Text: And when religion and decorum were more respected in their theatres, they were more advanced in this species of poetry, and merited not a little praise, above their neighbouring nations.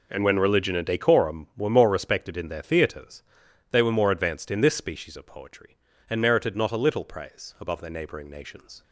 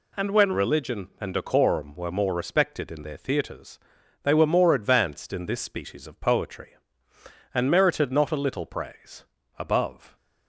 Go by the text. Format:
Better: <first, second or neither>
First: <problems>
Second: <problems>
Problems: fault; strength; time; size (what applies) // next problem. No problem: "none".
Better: first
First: none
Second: stops before "their neighbouring nations"; at 10.1 s